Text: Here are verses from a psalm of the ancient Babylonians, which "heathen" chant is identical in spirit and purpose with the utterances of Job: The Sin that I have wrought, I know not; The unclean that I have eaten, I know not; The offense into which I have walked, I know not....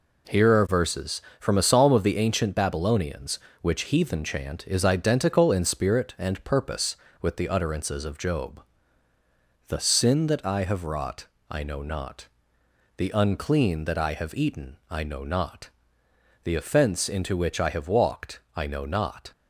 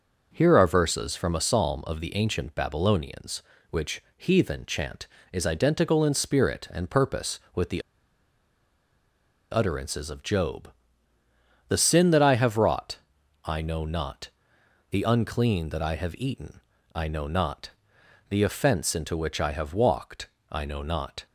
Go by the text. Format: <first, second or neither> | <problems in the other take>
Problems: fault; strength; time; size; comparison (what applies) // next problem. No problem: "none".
first | pauses between "the" and "utterances"; strong; at 7.8 s; 1.7 s long